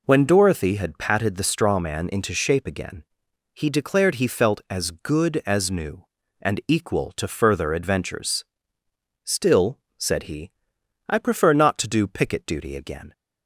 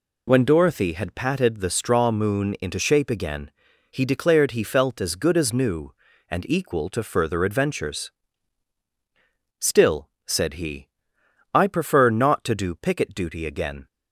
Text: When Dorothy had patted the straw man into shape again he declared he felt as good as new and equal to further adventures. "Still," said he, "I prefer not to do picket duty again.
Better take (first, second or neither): first